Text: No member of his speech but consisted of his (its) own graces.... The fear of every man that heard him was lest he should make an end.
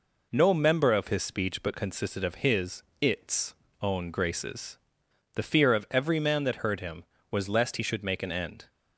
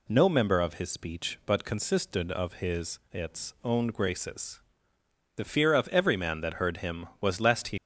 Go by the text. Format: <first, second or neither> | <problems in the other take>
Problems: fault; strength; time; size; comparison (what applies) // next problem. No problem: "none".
first | stops before "should make an end"; at 7.7 s